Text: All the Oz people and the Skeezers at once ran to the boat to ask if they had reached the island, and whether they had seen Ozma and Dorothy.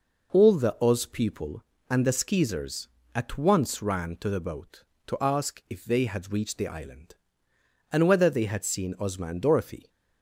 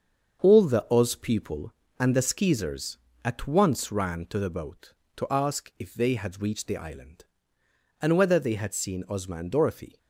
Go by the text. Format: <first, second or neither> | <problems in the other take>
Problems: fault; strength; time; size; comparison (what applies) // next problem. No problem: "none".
first | gets quieter; throughout; 6.5 dB